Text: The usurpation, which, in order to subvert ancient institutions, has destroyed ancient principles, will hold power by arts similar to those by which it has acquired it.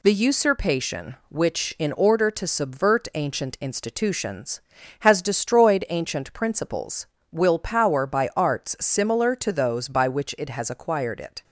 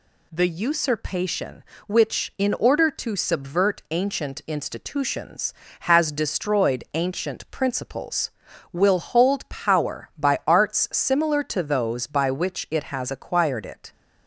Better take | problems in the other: second | skips "hold"; at 7.5 s

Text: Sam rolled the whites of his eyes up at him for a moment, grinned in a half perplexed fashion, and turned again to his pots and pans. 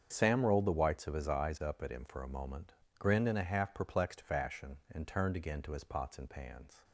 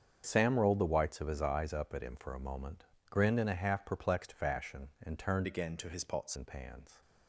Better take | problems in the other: first | starts louder than the rest; strong; until 1.2 s; 7 dB; strong in the first // changes voice from "again" to "pots"; from 5.4 to 6.3 s; 0.9 s long

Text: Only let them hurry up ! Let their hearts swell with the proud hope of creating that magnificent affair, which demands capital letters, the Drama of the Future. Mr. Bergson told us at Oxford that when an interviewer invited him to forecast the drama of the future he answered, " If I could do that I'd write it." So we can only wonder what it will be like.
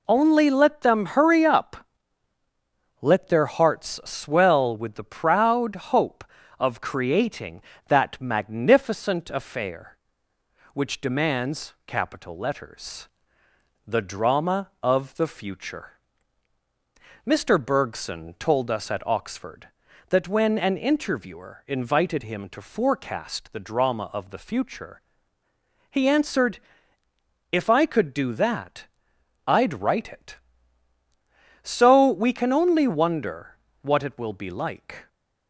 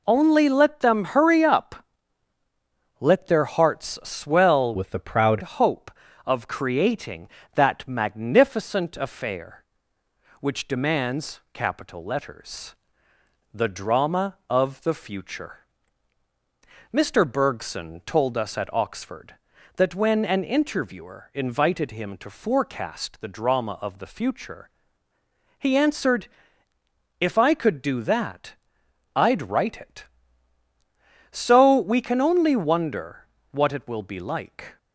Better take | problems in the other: first | changes voice from "with" to "proud"; from 4.7 to 5.4 s; 0.7 s long // pauses between "future" and "he"; noticeable; at 24.6 s; 0.90 s long; noticeable in the first // pauses between "that" and "I'd"; noticeable; at 28.5 s; 0.62 s long; noticeable in the first // pauses between "wonder" and "what"; slight; at 33.2 s; 0.26 s long; slight in the first

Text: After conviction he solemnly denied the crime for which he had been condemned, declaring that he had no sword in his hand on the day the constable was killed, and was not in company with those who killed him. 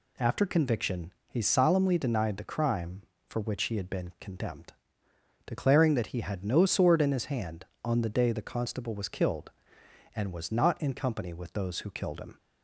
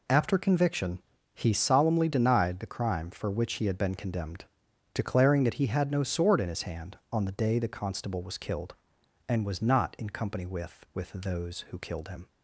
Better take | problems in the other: first | pauses between "conviction" and "he"; slight; at 1.0 s; 0.34 s long; slight in the first // says "with" twice; at 10.9 s

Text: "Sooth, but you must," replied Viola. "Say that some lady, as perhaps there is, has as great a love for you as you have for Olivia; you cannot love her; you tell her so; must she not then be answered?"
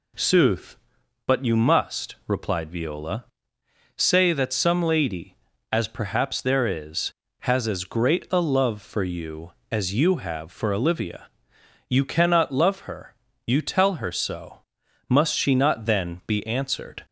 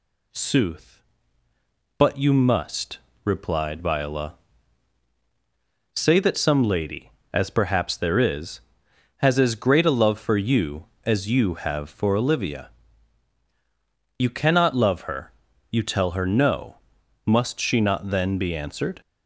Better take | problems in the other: first | says "no" for "so"; at 16.2 s

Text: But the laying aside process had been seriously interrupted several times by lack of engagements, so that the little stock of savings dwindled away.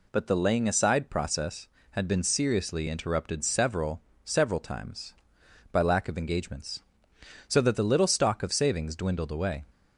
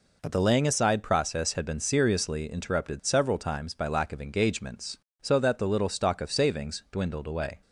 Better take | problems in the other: second | says "several" twice; at 4.2 s

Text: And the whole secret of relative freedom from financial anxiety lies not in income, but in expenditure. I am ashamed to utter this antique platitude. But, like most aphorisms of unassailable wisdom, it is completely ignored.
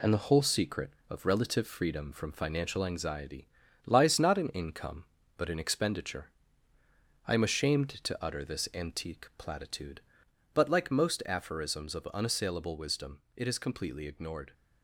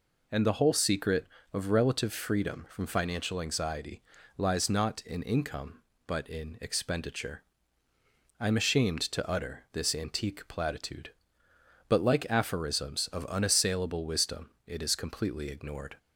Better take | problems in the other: first | pauses between "anxiety" and "lies"; slight; at 4.0 s; 0.36 s long; slight in the first // skips "most"; at 12.2 s

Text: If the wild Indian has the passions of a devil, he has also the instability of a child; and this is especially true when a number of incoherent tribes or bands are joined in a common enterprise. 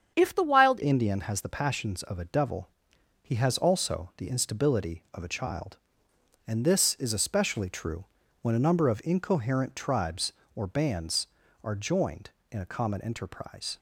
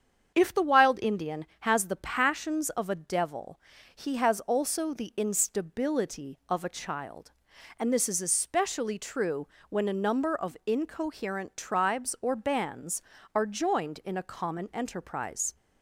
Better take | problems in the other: second | starts louder than the rest; strong; until 1.1 s; 7.5 dB; strong in the second // changes voice at "Indian"; from 0.8 s on; 12.9 s long // pauses between "true" and "when"; slight; at 8.0 s; 0.36 s long; slight in the second

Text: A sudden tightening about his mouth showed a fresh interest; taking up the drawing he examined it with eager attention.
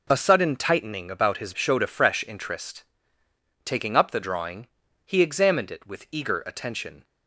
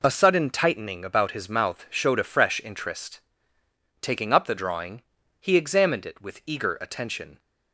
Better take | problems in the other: second | skips "mouth"; at 1.5 s // pauses between "drawing" and "he"; at 4.6 s; 0.40 s long; also in the second

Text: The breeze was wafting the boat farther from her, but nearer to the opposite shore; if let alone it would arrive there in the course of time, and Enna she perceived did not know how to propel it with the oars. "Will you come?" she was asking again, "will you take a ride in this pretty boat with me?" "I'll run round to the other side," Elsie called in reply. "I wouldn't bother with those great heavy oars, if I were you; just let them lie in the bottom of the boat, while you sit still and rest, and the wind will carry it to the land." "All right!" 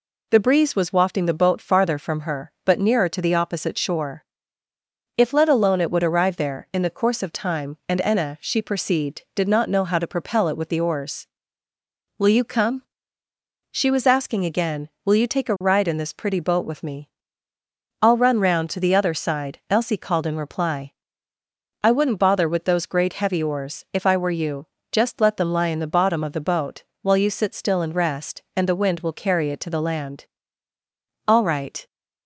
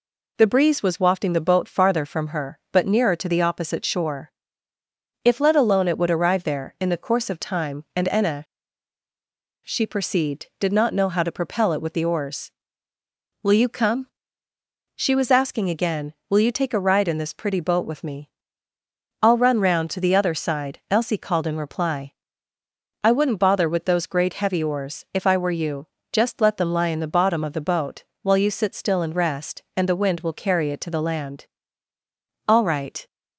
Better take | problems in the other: first | pauses between "Enna" and "she"; at 8.4 s; 1.2 s long

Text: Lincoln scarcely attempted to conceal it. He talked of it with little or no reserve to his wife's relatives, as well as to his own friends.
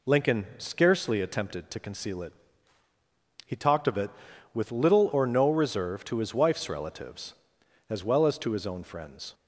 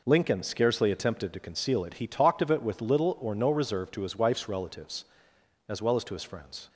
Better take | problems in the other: first | skips "own"; at 6.2 s

